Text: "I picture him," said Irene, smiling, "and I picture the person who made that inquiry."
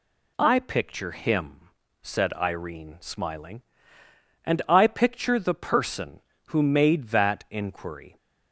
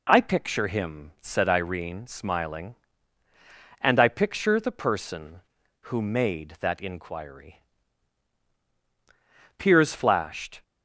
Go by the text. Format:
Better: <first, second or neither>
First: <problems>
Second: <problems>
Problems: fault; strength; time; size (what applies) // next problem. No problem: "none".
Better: first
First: none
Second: goes on to say "Piers flashed"; noticeable; from 9.5 s on; 1.0 s long